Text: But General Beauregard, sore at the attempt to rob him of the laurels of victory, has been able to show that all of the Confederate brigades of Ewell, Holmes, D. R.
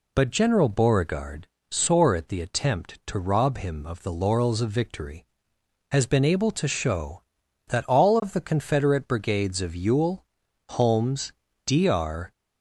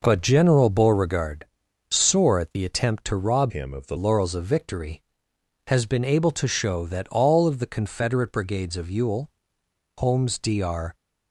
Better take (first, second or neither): first